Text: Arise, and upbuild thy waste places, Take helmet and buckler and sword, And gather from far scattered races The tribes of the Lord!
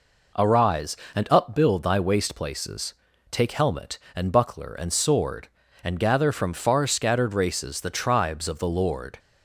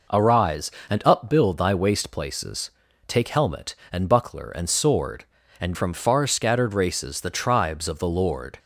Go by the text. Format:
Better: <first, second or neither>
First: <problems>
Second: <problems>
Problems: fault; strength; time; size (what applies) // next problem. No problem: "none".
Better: first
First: none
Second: skips "gather"; at 5.7 s